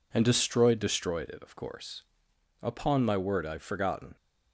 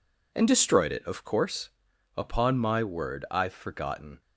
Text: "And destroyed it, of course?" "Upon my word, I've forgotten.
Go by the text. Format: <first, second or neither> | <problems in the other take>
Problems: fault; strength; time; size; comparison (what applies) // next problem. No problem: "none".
second | says "destroyed" twice; at 0.7 s